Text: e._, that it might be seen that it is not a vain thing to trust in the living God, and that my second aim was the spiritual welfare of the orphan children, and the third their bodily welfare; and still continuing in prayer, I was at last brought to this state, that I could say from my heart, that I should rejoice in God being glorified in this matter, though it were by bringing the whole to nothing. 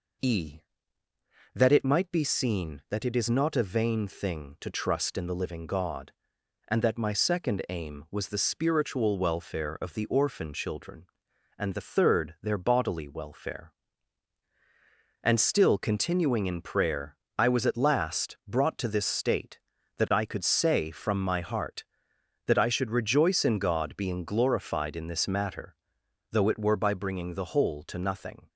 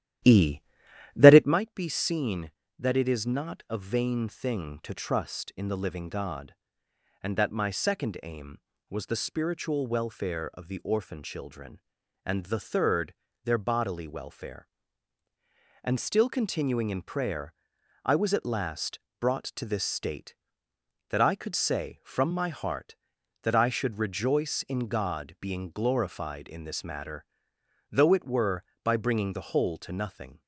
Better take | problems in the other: first | starts louder than the rest; strong; until 1.6 s; 12 dB // pauses between "third" and "their"; slight; at 13.1 s; 0.30 s long // pauses between "last" and "brought"; slight; at 18.9 s; 0.22 s long

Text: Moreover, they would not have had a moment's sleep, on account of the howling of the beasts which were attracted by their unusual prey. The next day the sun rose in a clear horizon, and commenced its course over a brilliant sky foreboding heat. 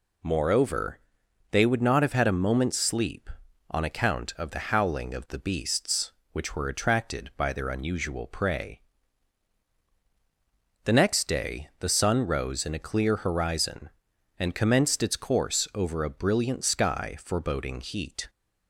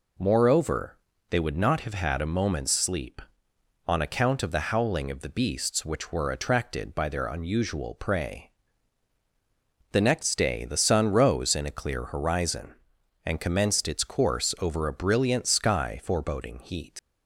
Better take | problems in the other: first | leaves "heat" unfinished; at 16.9 s; 85 ms

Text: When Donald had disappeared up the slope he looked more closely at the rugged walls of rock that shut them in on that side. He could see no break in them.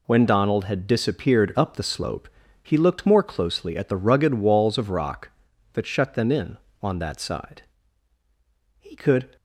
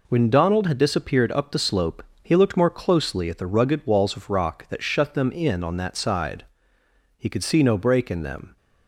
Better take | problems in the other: second | pauses between "slope" and "he"; slight; at 2.2 s; 0.34 s long; slight in the second // stops before "see no break in them"; at 9.3 s

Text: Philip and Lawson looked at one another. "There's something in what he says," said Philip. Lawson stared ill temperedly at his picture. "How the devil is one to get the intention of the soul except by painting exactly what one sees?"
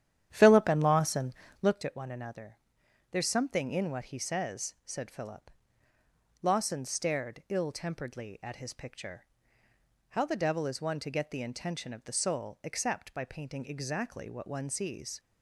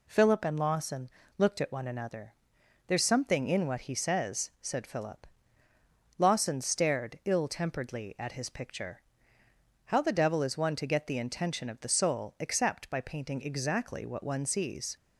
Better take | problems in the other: second | starts louder than the rest; strong; until 1.8 s; 10.5 dB // pauses between "Lawson" and "looked"; slight; at 1.3 s; 0.28 s long; slight in the second

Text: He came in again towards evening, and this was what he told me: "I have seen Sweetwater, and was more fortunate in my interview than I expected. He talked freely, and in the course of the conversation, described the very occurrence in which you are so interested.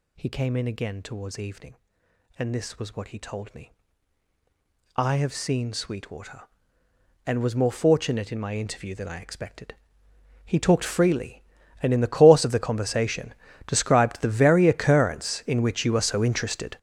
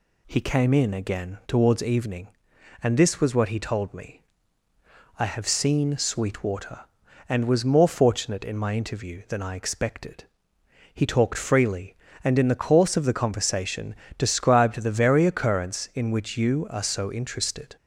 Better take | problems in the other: second | gets louder; strong; throughout; 12.5 dB

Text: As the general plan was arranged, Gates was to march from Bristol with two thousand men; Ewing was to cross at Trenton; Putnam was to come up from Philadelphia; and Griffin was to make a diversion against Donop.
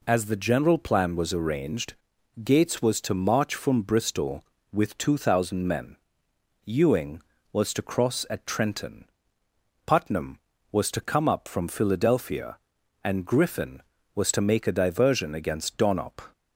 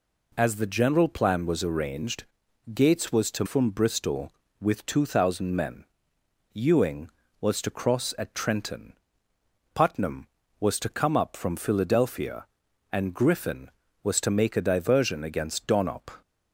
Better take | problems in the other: first | skips "march"; at 3.4 s

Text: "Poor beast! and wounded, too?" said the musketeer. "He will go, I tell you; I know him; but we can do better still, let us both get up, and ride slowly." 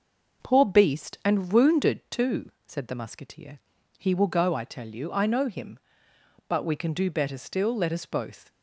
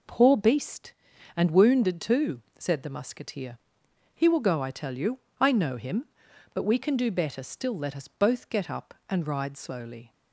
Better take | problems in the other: second | stops before "get up and ride slowly"; at 8.4 s

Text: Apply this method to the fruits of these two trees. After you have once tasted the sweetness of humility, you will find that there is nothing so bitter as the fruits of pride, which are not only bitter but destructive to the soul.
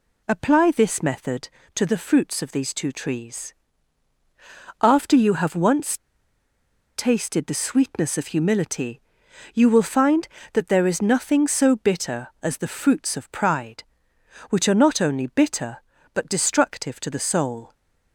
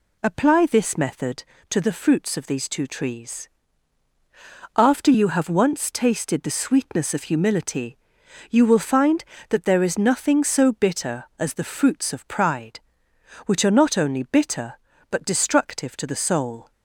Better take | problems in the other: second | pauses between "once" and "tasted"; at 5.9 s; 0.98 s long

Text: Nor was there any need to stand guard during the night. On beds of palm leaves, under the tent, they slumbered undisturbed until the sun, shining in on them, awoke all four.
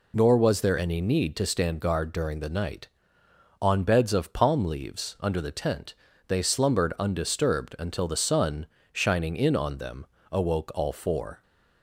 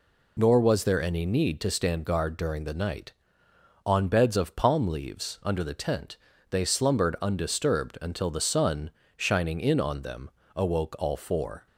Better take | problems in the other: neither | none

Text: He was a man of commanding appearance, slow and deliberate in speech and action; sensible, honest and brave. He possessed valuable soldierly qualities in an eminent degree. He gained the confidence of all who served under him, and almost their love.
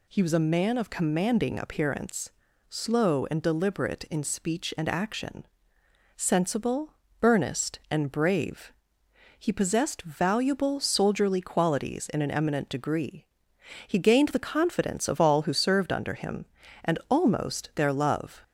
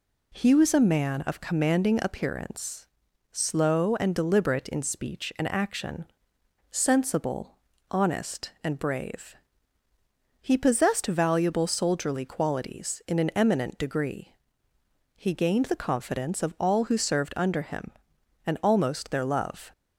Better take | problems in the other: second | says "earnest" for "honest"; at 7.2 s

